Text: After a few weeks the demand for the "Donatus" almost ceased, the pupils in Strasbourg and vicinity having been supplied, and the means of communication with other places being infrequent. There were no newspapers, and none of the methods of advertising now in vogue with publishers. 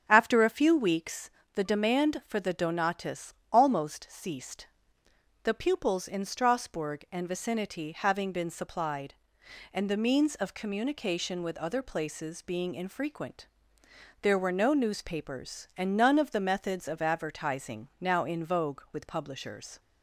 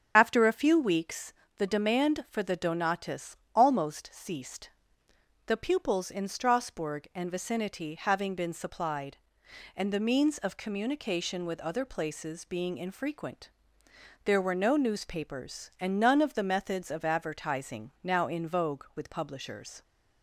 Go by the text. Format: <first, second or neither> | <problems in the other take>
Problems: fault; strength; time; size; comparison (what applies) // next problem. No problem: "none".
first | loses the start of "After"; at 0.1 s; 35 ms // starts louder than the rest; strong; until 1.1 s; 8 dB; strong in the first // pauses between "weeks" and "the"; slight; at 1.3 s; 0.24 s long; slight in the first // pauses between "Donatus" and "almost"; slight; at 3.3 s; 0.22 s long; slight in the first